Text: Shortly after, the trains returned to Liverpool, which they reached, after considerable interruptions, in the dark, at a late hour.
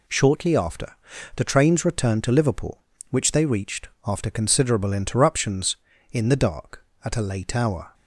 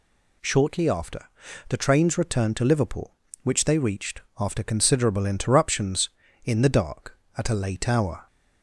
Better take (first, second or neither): second